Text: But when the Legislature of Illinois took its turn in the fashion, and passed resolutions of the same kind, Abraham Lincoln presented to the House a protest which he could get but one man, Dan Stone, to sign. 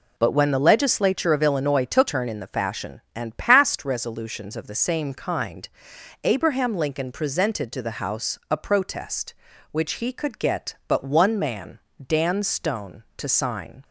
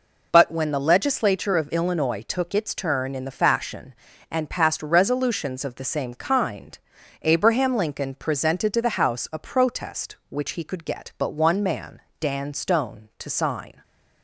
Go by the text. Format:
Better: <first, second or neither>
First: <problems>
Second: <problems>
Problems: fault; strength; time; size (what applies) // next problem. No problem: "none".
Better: second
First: skips "its"; at 2.0 s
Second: none